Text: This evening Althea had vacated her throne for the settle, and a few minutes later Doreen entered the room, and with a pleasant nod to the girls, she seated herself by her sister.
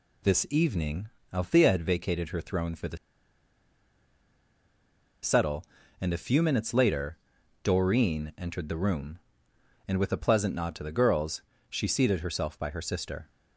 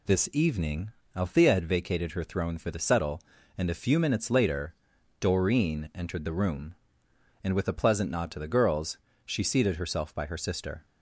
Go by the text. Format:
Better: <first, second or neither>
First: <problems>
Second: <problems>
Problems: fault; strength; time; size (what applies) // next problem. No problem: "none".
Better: second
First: pauses between "evening" and "Althea"; slight; at 1.0 s; 0.24 s long // pauses between "the" and "settle"; strong; at 2.9 s; 2.2 s long // pauses between "later" and "Doreen"; at 7.1 s; 0.44 s long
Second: pauses between "evening" and "Althea"; slight; at 0.9 s; 0.24 s long // pauses between "later" and "Doreen"; at 4.7 s; 0.44 s long